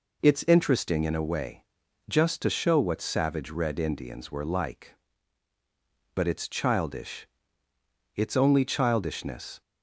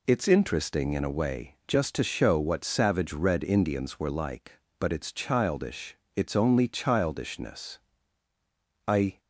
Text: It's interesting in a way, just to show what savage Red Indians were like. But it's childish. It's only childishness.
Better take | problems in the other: first | goes on to say "I"; slight; from 8.8 s on; 0.34 s long

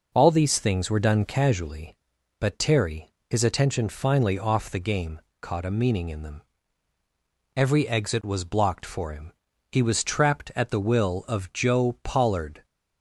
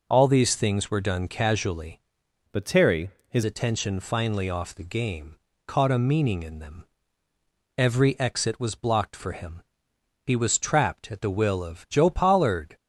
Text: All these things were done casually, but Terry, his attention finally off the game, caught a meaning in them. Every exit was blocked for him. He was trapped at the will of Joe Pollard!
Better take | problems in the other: first | changes voice from "but" to "his"; from 2.4 to 3.4 s; 1.0 s long

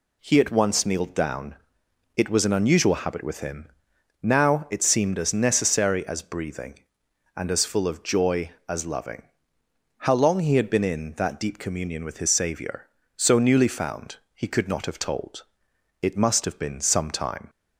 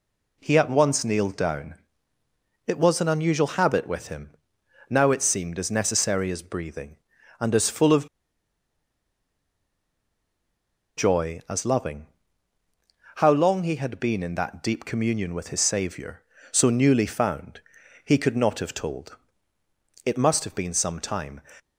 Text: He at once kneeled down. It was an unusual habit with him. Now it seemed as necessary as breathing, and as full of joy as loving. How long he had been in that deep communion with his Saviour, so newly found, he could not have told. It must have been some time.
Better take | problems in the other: first | pauses between "of" and "joy"; strong; at 8.0 s; 2.8 s long

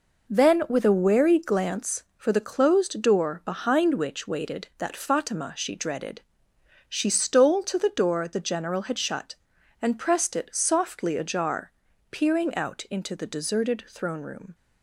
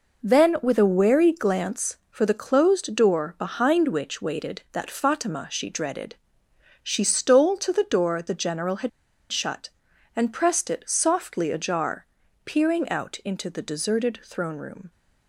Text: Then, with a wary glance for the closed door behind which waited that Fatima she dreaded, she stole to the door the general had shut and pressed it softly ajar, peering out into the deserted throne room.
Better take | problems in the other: first | pauses between "had" and "shut"; at 8.8 s; 0.42 s long

